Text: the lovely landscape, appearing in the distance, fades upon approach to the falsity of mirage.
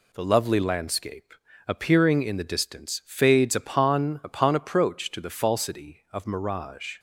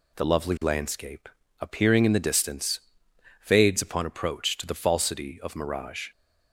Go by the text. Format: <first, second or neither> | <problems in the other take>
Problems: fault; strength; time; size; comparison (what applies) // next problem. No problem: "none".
second | says "upon" twice; at 4.2 s